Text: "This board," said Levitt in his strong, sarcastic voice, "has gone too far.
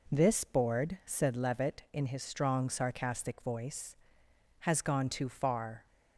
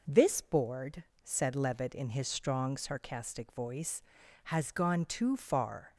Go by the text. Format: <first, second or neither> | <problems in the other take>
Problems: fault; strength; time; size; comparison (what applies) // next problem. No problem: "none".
neither | none